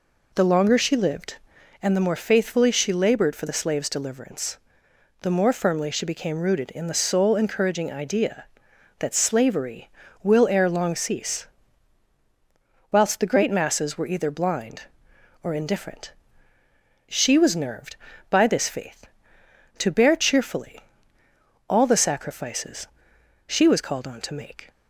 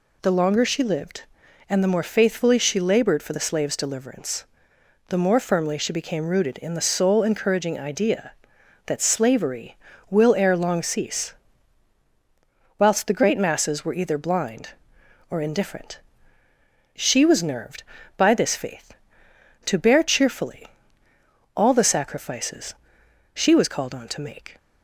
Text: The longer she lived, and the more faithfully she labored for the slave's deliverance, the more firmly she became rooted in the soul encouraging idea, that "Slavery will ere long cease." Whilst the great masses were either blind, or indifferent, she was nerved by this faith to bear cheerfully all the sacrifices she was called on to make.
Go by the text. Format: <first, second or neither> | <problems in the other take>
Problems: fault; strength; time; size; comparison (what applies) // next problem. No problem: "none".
second | starts louder than the rest; until 1.8 s; 3.5 dB // pauses between "cheerfully" and "all"; noticeable; at 20.8 s; 0.88 s long; noticeable in the second // pauses between "sacrifices" and "she"; noticeable; at 22.8 s; 0.60 s long; noticeable in the second